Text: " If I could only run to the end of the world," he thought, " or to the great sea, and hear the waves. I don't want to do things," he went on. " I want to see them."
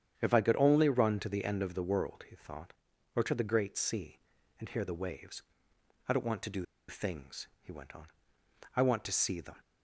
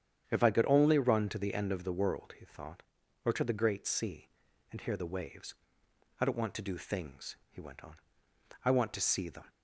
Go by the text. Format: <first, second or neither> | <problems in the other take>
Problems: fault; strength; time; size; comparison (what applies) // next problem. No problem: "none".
second | starts louder than the rest; strong; until 1.1 s; 8.5 dB; strong in the second // pauses between "do" and "things"; slight; at 6.6 s; 0.24 s long